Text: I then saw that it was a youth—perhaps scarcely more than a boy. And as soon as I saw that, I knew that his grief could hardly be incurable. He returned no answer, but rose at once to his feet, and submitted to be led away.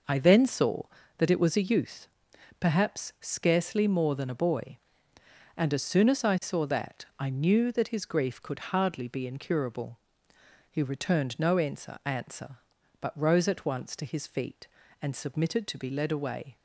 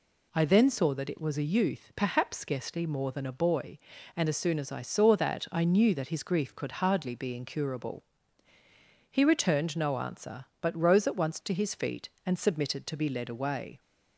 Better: second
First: says "answer" twice; at 12.0 s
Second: none

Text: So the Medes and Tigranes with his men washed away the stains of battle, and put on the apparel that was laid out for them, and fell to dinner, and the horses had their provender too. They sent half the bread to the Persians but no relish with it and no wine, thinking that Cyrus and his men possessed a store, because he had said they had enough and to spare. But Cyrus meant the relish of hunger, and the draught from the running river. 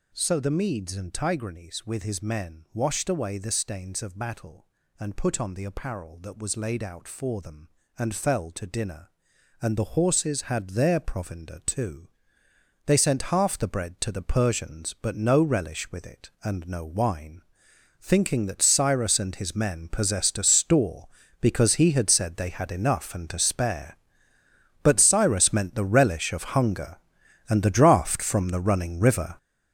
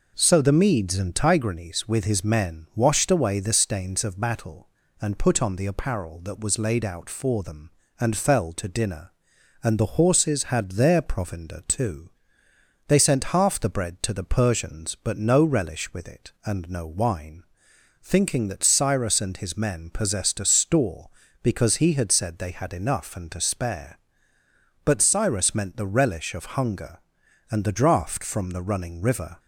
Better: second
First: gets louder; strong; throughout; 10 dB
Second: none

